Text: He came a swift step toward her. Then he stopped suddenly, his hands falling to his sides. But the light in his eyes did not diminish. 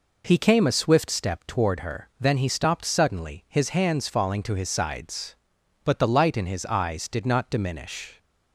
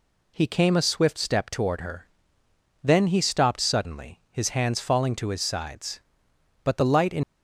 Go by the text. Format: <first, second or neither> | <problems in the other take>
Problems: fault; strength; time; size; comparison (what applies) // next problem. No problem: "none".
first | stops before "his eyes did not diminish"; at 7.2 s